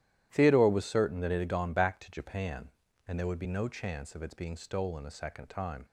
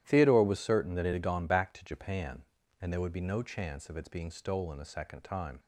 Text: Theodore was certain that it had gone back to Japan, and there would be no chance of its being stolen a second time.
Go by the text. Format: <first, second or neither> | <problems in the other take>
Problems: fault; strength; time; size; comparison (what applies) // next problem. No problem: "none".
neither | starts louder than the rest; strong; the same in both